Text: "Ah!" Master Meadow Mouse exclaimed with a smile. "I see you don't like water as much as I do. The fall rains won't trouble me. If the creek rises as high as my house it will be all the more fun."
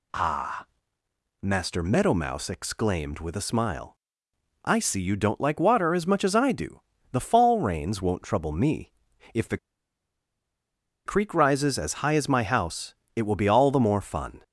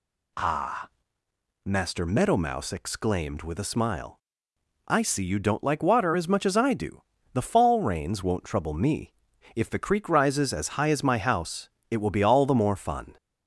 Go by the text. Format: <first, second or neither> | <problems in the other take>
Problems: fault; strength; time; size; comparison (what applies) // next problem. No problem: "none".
second | pauses between "the" and "creek"; strong; at 9.5 s; 1.4 s long // pauses between "house" and "it"; slight; at 12.9 s; 0.22 s long; slight in the second